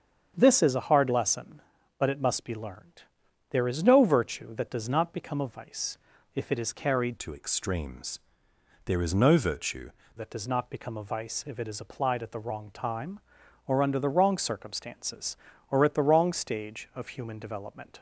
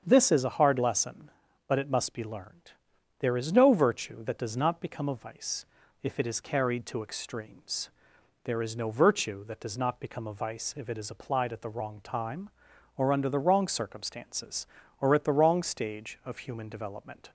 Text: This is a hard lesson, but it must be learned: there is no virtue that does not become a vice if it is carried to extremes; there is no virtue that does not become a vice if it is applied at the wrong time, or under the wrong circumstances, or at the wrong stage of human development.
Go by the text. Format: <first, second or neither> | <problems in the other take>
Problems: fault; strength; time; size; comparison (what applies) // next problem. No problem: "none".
second | starts louder than the rest; strong; until 1.3 s; 8 dB; strong in the second // pauses between "vice" and "if"; at 5.9 s; 0.38 s long; also in the second // changes voice from "to" to "virtue"; from 7.1 to 9.9 s; 2.8 s long